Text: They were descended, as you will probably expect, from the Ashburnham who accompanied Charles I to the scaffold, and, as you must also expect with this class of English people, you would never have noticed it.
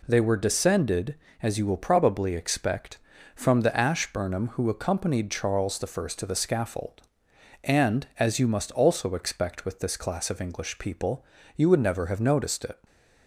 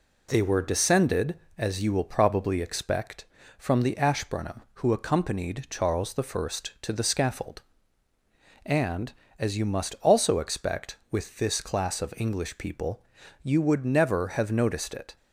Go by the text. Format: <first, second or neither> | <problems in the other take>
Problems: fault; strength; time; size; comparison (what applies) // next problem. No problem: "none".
neither | none